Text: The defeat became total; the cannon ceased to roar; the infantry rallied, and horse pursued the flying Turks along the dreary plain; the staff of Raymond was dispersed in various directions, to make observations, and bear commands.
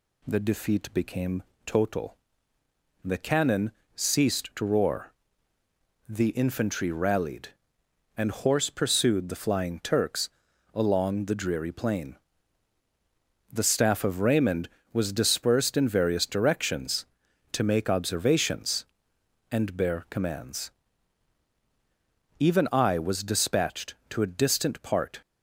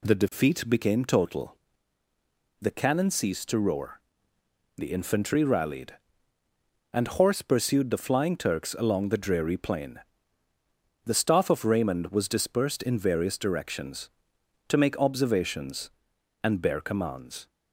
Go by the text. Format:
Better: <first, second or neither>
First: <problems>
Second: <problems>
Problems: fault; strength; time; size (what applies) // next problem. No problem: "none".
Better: second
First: pauses between "became" and "total"; slight; at 1.4 s; 0.24 s long // pauses between "cannon" and "ceased"; slight; at 3.7 s; 0.24 s long // pauses between "Turks" and "along"; noticeable; at 10.2 s; 0.46 s long // goes on to say "Even I was dispatched to a distant part"; strong; from 22.3 s on; 2.8 s long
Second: none